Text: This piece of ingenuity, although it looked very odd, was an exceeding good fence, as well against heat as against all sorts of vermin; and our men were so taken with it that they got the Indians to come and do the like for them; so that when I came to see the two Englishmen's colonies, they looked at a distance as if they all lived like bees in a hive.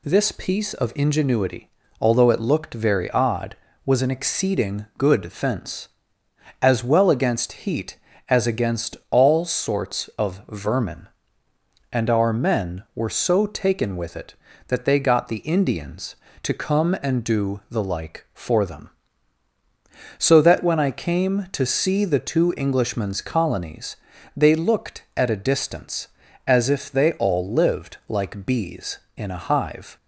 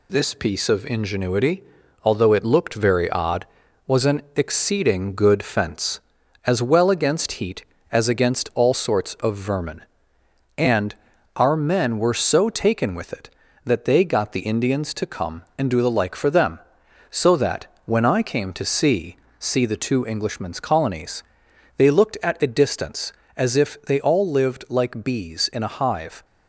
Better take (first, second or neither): first